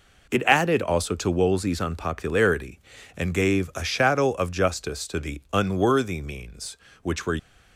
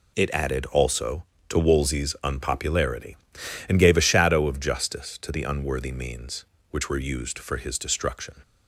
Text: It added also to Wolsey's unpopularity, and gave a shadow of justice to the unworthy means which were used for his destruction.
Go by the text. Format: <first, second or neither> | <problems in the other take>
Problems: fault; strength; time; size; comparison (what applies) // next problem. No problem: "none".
second | stops before "used for his destruction"; at 7.3 s